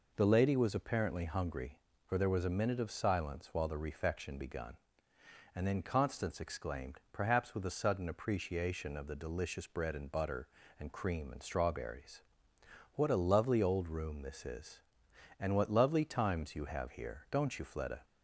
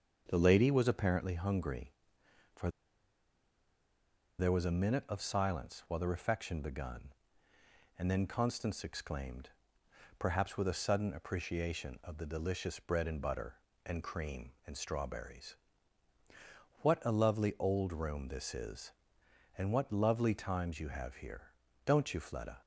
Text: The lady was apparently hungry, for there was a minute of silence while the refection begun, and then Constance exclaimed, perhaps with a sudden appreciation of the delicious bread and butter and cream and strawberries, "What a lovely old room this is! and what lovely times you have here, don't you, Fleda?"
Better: first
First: none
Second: starts louder than the rest; until 1.2 s; 7 dB // pauses between "for" and "there"; strong; at 2.6 s; 1.7 s long

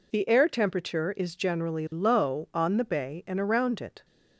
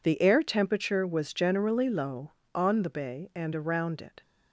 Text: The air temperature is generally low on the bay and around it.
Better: first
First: none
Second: says "was" for "is"; at 1.0 s

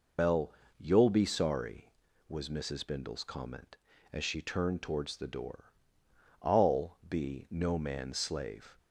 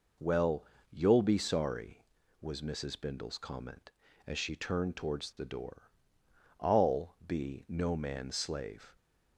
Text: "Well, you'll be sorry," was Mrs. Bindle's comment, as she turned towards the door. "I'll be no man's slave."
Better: second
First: loses the start of "Well"; at 0.1 s; 115 ms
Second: none

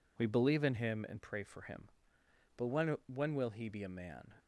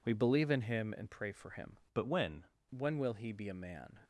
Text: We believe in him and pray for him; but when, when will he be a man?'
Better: first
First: none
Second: changes voice from "but" to "when"; from 1.9 to 2.4 s; 0.5 s long

